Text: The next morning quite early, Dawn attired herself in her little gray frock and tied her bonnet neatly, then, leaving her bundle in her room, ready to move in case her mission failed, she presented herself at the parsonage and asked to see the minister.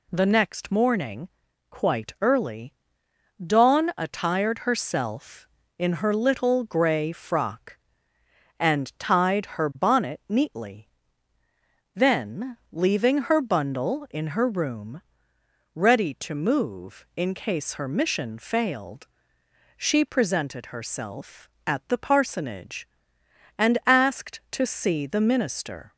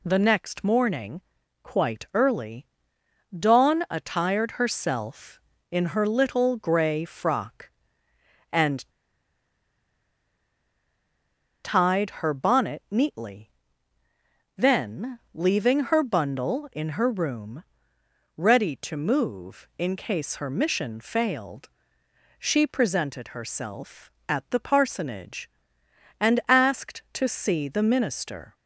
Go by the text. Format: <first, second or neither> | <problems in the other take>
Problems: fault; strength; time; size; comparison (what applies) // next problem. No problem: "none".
first | pauses between "morning" and "quite"; at 1.2 s; 0.42 s long; also in the first // pauses between "and" and "tied"; strong; at 8.8 s; 2.7 s long